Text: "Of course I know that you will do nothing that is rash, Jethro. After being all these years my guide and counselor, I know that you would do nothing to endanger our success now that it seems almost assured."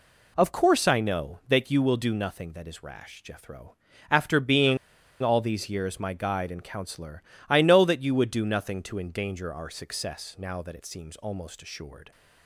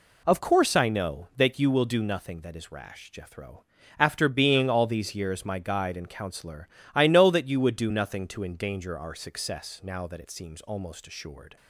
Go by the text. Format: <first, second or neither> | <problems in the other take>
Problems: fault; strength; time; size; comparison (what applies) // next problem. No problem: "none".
second | pauses between "being" and "all"; at 4.7 s; 0.45 s long